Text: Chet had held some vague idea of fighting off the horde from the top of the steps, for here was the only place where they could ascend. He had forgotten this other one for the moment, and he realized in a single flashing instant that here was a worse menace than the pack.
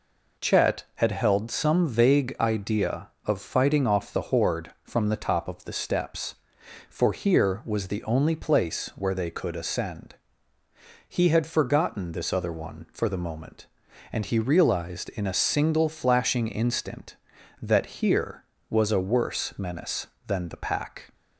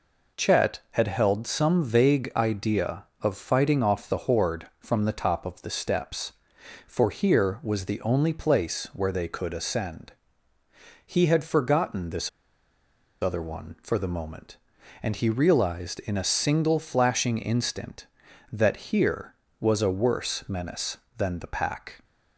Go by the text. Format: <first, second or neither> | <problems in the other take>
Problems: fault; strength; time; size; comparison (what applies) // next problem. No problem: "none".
first | pauses between "this" and "other"; noticeable; at 12.2 s; 0.91 s long // pauses between "that" and "here"; slight; at 18.7 s; 0.16 s long; slight in the first